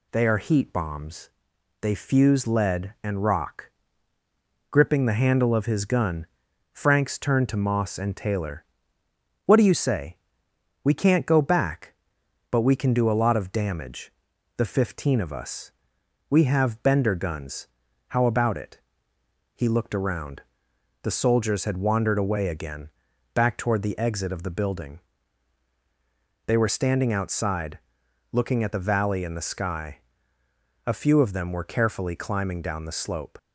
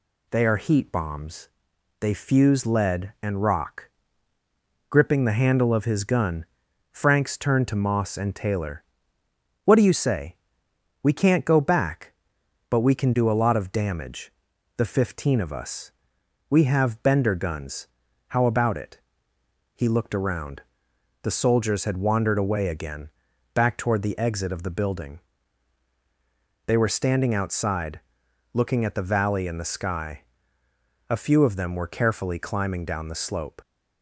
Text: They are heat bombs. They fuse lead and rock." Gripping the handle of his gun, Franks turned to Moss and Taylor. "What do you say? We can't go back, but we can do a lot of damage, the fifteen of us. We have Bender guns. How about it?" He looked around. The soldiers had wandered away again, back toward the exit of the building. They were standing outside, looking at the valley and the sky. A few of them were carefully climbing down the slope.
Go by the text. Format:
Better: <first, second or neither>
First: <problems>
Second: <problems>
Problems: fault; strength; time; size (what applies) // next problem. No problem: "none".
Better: neither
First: none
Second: none